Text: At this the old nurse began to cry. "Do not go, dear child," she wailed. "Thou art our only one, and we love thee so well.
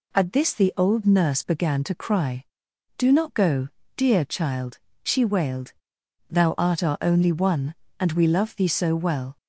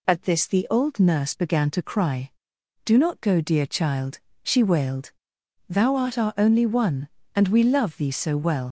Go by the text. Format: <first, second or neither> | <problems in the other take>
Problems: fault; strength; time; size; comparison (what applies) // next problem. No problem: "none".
first | leaves "well" unfinished; at 8.6 s; 95 ms